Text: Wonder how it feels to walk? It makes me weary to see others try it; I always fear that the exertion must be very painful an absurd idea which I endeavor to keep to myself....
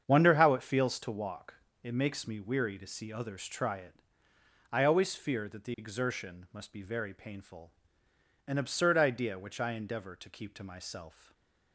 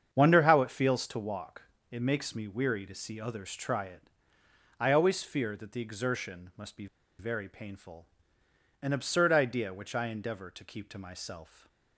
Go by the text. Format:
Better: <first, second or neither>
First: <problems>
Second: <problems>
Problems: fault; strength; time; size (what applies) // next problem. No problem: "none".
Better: first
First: starts louder than the rest; strong; until 1.0 s; 7.5 dB // pauses between "painful" and "an"; noticeable; at 7.7 s; 0.76 s long // stays silent after the last word; slight; from 11.1 s on; 0.6 s long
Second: starts louder than the rest; strong; until 1.1 s; 7.5 dB // pauses between "be" and "very"; slight; at 6.8 s; 0.33 s long // pauses between "painful" and "an"; noticeable; at 8.0 s; 0.76 s long // stays silent after the last word; slight; from 11.4 s on; 0.5 s long